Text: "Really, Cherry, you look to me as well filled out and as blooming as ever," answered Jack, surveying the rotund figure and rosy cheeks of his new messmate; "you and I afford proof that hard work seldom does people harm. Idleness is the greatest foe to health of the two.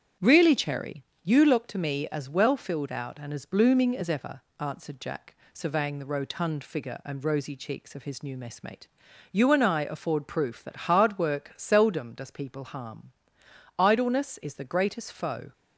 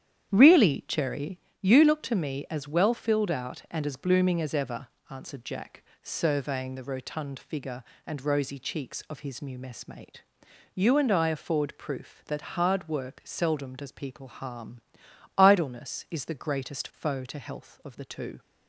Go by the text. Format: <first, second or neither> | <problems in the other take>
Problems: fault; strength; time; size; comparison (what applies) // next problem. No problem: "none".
second | starts louder than the rest; strong; until 1.3 s; 8.5 dB; strong in the second // stops before "to health of the two"; at 15.5 s